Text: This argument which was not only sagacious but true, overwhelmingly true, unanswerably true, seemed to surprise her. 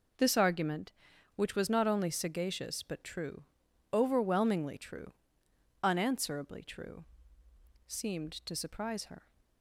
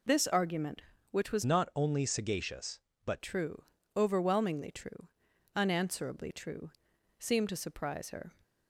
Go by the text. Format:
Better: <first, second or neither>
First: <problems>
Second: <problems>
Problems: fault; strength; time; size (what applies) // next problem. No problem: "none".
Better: first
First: none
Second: changes voice from "not" to "but"; from 1.4 to 3.2 s; 1.8 s long